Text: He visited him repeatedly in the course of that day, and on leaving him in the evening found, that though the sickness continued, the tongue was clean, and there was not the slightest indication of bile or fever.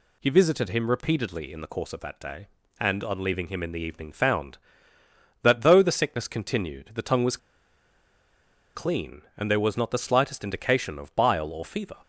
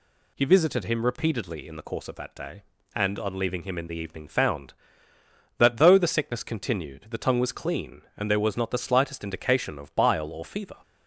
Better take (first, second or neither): second